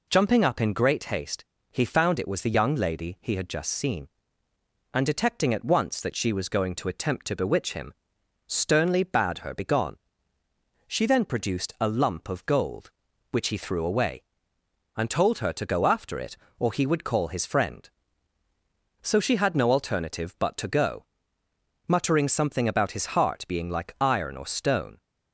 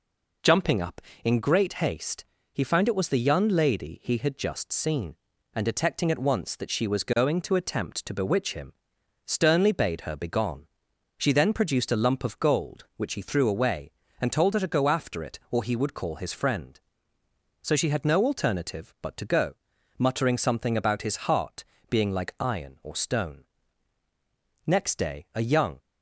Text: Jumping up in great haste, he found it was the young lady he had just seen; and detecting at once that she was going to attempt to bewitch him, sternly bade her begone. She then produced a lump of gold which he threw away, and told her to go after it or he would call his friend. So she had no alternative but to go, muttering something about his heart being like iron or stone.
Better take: first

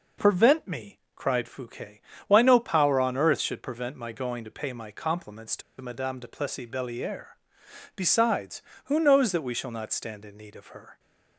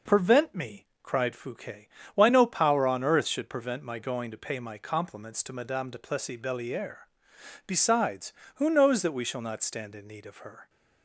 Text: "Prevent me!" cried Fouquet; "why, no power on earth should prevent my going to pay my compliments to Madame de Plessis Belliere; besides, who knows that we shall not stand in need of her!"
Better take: second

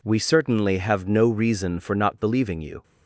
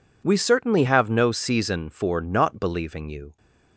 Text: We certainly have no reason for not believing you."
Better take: first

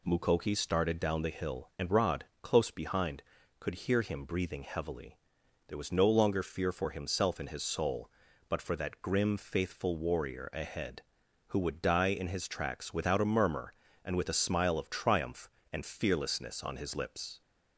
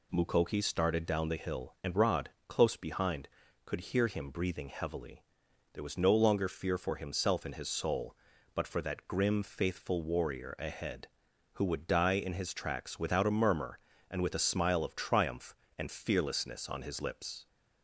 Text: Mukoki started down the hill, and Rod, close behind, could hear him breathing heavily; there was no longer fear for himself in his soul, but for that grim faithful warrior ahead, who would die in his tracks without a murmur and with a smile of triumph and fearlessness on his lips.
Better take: neither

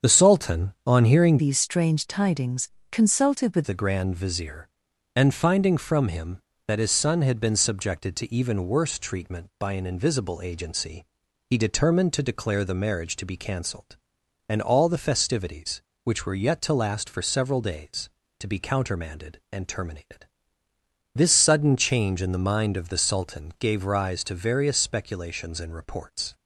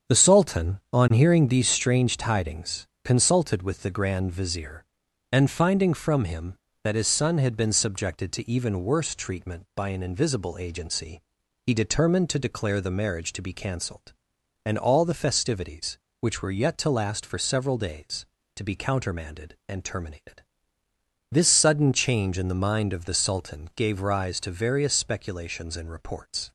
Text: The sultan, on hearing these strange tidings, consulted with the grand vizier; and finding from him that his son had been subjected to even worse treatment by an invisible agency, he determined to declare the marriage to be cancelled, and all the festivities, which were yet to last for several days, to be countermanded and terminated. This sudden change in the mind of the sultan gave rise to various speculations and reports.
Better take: second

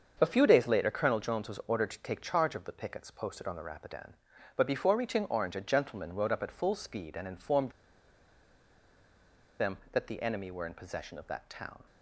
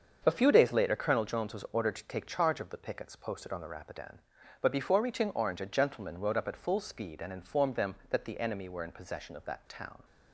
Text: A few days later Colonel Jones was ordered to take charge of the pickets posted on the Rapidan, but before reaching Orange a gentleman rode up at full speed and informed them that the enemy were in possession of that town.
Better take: second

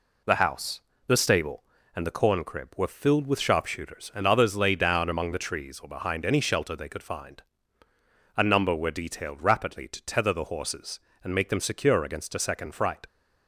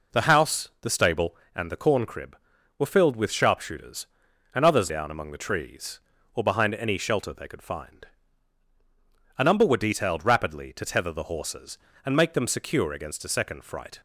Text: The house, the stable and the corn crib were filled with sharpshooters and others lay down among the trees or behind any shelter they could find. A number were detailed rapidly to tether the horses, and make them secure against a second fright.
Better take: first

